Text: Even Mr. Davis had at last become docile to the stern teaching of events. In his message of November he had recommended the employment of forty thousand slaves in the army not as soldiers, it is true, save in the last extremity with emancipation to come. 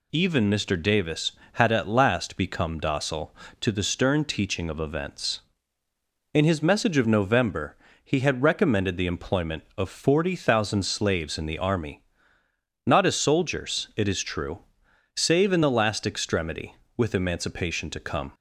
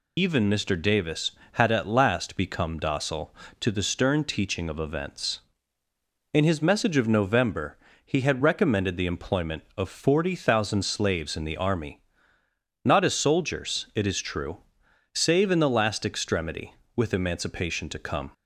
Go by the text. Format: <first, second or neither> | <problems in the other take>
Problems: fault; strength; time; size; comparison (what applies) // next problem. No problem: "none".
first | loses the start of "Even"; at 0.1 s; 55 ms // pauses between "November" and "he"; slight; at 7.7 s; 0.26 s long; slight in the first // pauses between "army" and "not"; noticeable; at 12.0 s; 0.84 s long; noticeable in the first